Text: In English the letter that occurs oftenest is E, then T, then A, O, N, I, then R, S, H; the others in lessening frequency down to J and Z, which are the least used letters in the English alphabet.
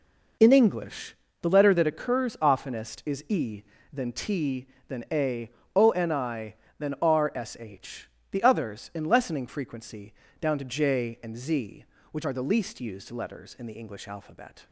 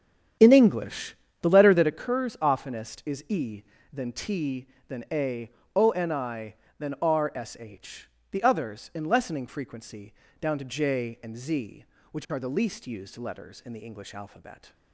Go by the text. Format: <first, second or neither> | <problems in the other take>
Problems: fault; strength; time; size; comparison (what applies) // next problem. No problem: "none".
first | starts louder than the rest; strong; until 2.1 s; 9 dB // pauses between "English" and "the"; slight; at 1.1 s; 0.28 s long; slight in the first // pauses between "frequency" and "down"; slight; at 10.1 s; 0.26 s long; slight in the first